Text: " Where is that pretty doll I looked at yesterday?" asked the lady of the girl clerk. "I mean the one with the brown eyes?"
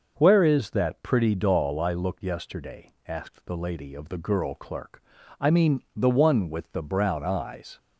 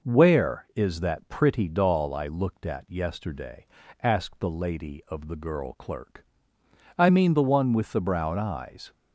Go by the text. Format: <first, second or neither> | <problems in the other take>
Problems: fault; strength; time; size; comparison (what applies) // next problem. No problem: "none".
second | skips "at"; at 2.2 s